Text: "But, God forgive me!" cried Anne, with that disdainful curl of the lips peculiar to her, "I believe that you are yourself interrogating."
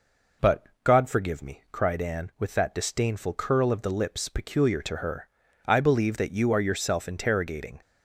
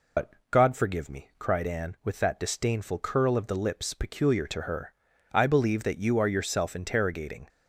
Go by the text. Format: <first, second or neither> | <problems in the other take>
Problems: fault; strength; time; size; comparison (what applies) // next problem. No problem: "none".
first | loses the start of "But"; at 0.1 s; 90 ms